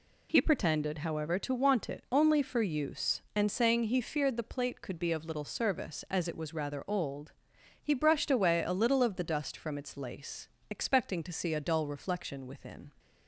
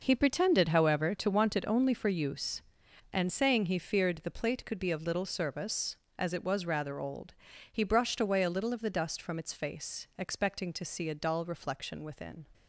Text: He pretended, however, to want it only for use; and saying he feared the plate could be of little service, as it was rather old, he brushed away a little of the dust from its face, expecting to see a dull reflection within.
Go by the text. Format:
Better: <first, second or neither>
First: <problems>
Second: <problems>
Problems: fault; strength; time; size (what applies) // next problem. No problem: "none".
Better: second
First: says "lace" for "face"; at 9.9 s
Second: none